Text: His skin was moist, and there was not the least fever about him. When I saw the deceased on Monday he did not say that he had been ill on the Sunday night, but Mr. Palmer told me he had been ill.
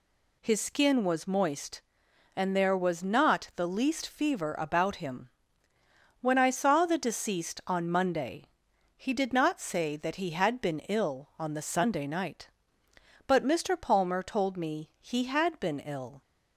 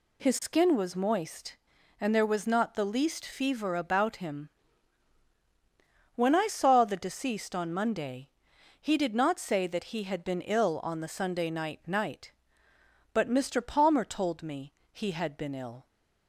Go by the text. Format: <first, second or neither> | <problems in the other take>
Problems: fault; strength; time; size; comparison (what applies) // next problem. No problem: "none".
first | pauses between "Monday" and "he"; noticeable; at 8.2 s; 0.50 s long; noticeable in the first // says "night" twice; at 11.8 s // pauses between "me" and "he"; slight; at 14.7 s; 0.22 s long